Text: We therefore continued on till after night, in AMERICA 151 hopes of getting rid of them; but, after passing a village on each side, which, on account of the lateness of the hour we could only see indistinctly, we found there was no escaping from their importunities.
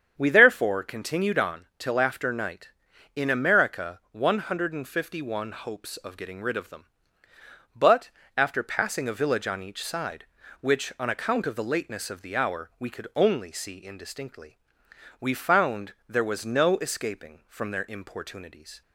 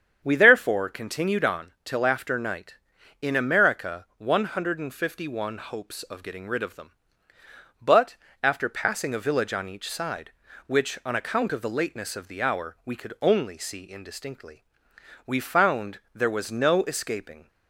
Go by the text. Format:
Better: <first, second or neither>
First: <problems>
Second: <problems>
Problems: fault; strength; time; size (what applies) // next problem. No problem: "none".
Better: first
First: starts louder than the rest; strong; until 1.1 s; 8 dB // pauses between "found" and "there"; slight; at 15.9 s; 0.16 s long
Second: starts louder than the rest; strong; until 1.2 s; 8 dB // pauses between "found" and "there"; slight; at 15.9 s; 0.16 s long // stops before "from their importunities"; at 17.4 s